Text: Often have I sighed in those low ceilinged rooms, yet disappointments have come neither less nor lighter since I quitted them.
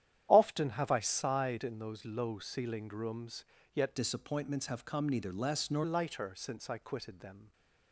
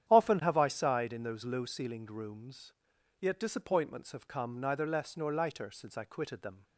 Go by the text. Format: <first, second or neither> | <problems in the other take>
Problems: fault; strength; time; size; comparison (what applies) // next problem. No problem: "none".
second | starts louder than the rest; strong; until 1.3 s; 10.5 dB; strong in the second // changes voice from "disappointments" to "nor"; from 3.9 to 5.8 s; 1.9 s long